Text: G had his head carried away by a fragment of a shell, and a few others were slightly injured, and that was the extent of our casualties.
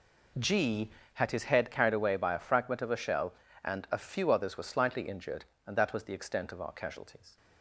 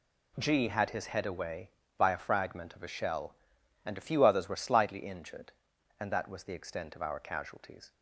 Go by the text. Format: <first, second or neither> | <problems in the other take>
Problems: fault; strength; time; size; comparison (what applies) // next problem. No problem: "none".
first | skips "carried"; at 1.2 s